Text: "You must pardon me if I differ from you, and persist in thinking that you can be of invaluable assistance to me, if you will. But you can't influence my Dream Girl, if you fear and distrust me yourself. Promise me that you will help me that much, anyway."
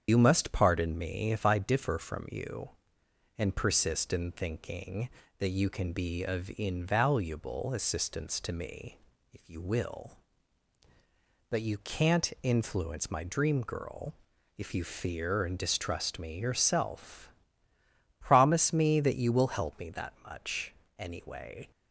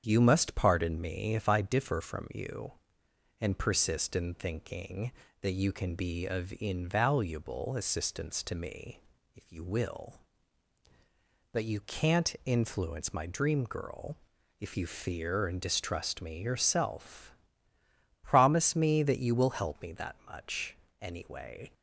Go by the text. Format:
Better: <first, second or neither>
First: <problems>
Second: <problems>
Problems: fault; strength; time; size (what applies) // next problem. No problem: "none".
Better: second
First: loses the start of "You"; at 0.0 s; 80 ms // starts louder than the rest; strong; until 1.0 s; 8 dB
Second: starts louder than the rest; strong; until 1.0 s; 8 dB